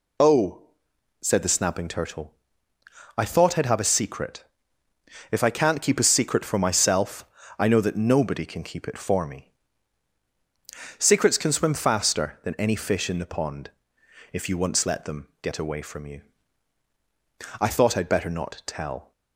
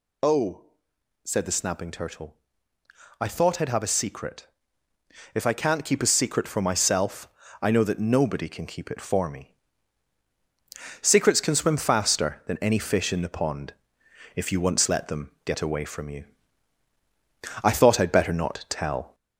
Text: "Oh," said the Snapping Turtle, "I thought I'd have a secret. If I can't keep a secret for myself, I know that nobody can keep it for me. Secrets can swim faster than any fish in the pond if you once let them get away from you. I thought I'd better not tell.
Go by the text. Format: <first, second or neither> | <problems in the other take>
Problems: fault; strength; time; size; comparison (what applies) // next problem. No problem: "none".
first | gets louder; slight; throughout; 2.5 dB // pauses between "pond" and "if"; noticeable; at 13.7 s; 0.62 s long; noticeable in the first